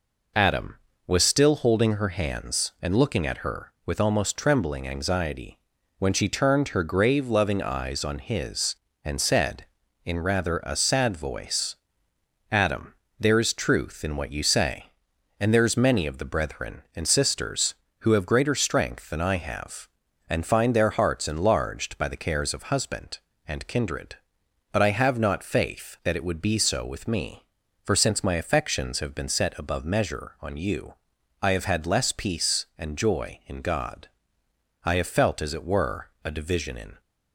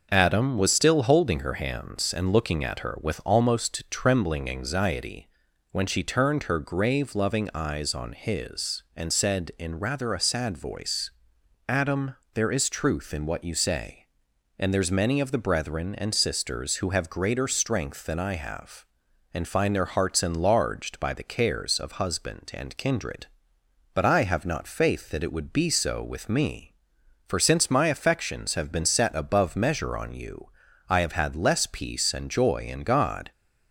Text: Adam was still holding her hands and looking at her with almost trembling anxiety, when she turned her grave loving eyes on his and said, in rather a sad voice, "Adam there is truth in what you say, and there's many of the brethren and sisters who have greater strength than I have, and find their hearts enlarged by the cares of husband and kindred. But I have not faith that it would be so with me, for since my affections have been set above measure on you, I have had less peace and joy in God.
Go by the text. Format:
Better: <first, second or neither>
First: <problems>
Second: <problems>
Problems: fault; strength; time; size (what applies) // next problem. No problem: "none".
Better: second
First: pauses between "Adam" and "there"; slight; at 12.9 s; 0.26 s long // goes on to say "I have felt as it were a division in"; strong; from 34.8 s on; 2.1 s long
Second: pauses between "Adam" and "there"; slight; at 12.1 s; 0.20 s long